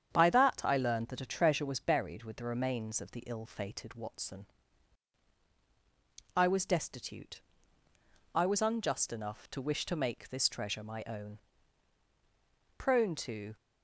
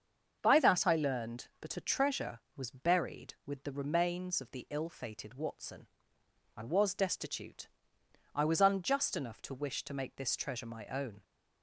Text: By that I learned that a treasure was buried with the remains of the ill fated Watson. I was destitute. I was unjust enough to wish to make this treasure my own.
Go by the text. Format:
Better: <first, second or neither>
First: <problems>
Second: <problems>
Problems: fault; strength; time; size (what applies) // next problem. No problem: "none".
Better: second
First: starts louder than the rest; strong; until 1.1 s; 8 dB // goes on to say "Prone to"; noticeable; from 12.7 s on; 0.78 s long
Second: starts louder than the rest; until 1.4 s; 7 dB